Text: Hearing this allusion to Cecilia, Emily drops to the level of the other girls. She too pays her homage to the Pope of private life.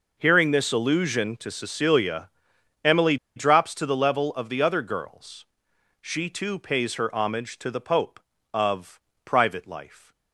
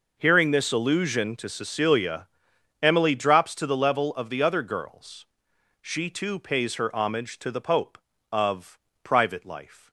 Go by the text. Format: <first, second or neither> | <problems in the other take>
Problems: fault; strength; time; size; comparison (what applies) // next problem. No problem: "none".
second | pauses between "Emily" and "drops"; slight; at 3.1 s; 0.19 s long // pauses between "of" and "private"; slight; at 8.9 s; 0.24 s long; slight in the second